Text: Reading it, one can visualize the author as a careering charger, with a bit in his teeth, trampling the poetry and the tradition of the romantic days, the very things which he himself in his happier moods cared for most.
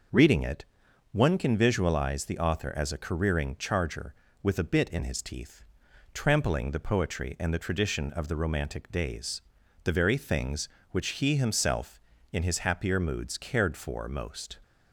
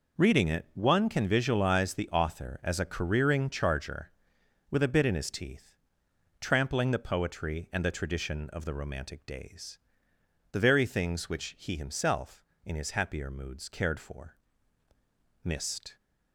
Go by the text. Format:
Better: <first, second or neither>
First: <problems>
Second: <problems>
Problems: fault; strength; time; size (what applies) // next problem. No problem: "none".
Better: first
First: none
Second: says "mist" for "most"; at 15.4 s